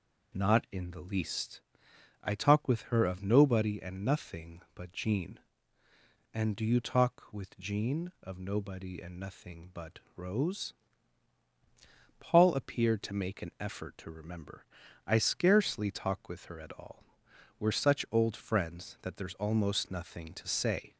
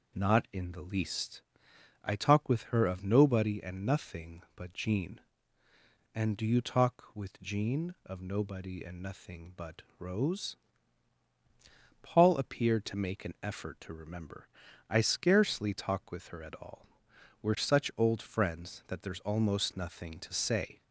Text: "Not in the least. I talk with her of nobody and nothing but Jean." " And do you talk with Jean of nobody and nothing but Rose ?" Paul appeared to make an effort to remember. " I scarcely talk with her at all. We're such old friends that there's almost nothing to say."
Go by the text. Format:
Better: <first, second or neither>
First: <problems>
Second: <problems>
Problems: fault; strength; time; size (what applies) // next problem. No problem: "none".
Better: neither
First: pauses between "but" and "Rose"; slight; at 10.0 s; 0.16 s long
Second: pauses between "but" and "Rose"; slight; at 9.8 s; 0.16 s long